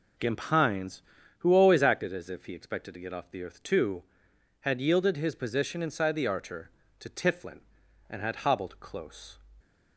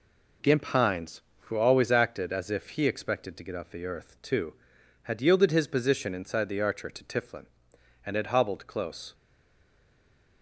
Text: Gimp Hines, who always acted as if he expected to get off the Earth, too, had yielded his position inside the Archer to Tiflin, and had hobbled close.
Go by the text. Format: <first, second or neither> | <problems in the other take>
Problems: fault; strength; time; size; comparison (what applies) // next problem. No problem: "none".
first | stays silent after the last word; noticeable; from 9.1 s on; 1.3 s long